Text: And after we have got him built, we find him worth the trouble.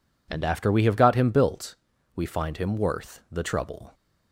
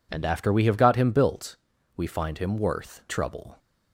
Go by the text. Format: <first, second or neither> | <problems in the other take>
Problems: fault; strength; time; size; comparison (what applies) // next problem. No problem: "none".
first | skips "the"; at 3.0 s